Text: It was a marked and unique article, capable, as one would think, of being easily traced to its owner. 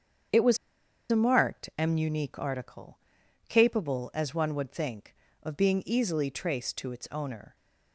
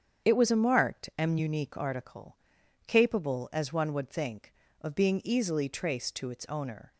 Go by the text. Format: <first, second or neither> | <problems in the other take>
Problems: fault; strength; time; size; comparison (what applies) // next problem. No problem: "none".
second | starts louder than the rest; strong; until 1.9 s; 8 dB; strong in the second // pauses between "was" and "a"; noticeable; at 0.5 s; 0.54 s long